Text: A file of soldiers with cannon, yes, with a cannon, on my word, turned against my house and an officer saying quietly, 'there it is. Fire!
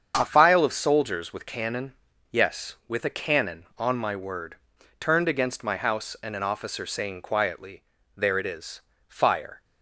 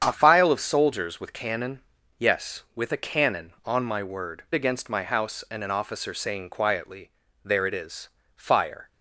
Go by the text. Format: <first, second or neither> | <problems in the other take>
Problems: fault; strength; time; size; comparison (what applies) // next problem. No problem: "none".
first | starts louder than the rest; strong; until 1.0 s; 8 dB; strong in the first // skips "turned"; at 4.4 s